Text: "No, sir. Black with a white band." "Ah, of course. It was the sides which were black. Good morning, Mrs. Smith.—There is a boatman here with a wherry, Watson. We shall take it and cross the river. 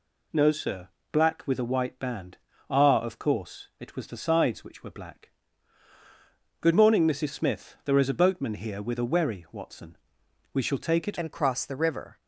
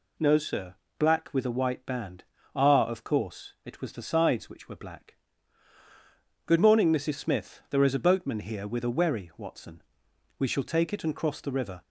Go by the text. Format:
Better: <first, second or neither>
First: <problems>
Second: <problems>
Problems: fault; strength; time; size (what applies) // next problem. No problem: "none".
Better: second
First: changes voice at "and"; from 11.1 s on; 1.1 s long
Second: none